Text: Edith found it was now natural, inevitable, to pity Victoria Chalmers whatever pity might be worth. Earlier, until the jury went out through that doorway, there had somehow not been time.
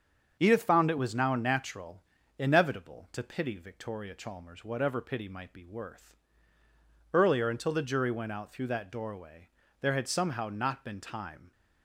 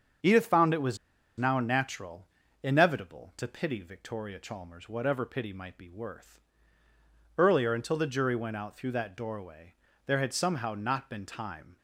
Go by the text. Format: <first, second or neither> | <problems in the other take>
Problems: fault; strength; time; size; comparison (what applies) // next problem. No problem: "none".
first | starts louder than the rest; strong; until 1.6 s; 7 dB; strong in the first // pauses between "was" and "now"; at 0.9 s; 0.41 s long